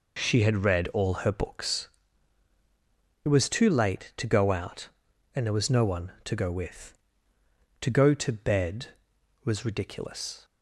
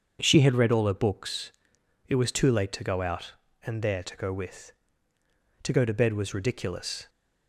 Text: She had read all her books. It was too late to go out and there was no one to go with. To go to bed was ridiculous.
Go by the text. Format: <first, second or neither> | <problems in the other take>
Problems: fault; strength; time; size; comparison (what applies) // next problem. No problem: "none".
first | starts louder than the rest; until 1.2 s; 7 dB // skips "was no one"; at 4.0 s